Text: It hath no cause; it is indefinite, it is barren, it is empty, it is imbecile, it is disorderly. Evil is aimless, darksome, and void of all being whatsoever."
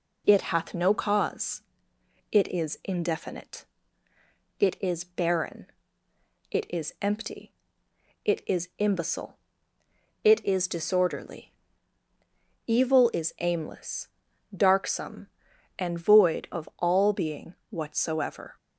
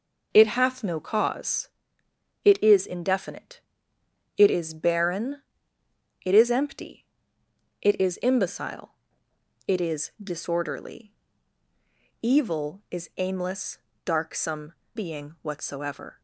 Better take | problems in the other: first | skips "and void of all"; at 14.8 s

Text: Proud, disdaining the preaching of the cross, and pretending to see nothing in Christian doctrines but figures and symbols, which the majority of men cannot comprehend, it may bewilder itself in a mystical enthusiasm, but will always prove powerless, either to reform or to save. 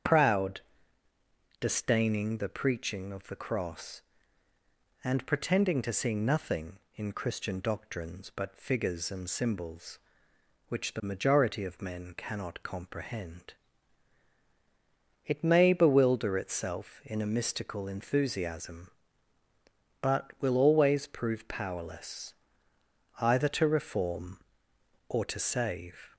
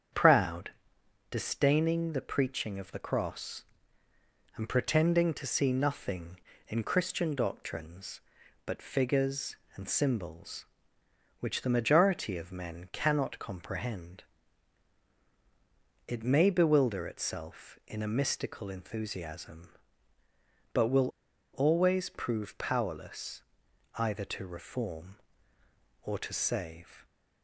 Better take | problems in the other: first | starts louder than the rest; strong; until 1.7 s; 8 dB; strong in the first // pauses between "will" and "always"; at 21.0 s; 0.44 s long

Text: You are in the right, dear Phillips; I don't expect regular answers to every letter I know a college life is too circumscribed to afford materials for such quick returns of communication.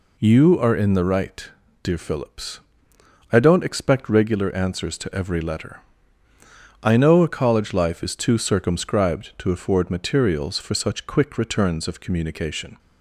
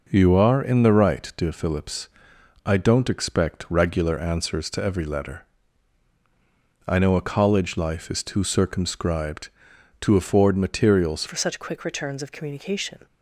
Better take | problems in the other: first | pauses between "letter" and "I"; strong; at 5.4 s; 1.4 s long; also in the first // changes voice at "for"; from 11.2 s on; 1.8 s long

